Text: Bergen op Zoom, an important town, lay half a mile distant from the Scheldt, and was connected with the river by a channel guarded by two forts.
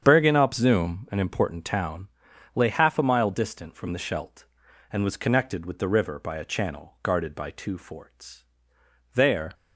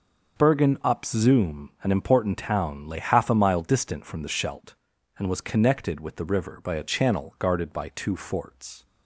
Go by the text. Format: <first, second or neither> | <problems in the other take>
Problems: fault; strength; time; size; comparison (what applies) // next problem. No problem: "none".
second | starts louder than the rest; strong; until 1.0 s; 8 dB; also in the second // goes on to say "There"; slight; from 9.1 s on; 0.40 s long